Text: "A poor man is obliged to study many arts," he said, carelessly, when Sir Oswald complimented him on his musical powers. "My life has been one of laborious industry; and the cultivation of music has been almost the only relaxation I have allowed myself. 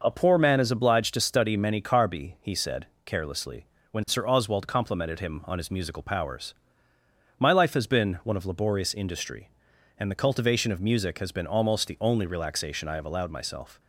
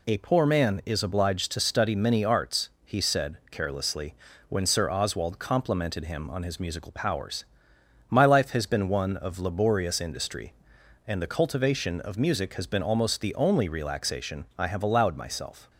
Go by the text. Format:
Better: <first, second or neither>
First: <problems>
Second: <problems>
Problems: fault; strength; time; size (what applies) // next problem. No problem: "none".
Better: second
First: says "carbi" for "arts"; at 1.7 s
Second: none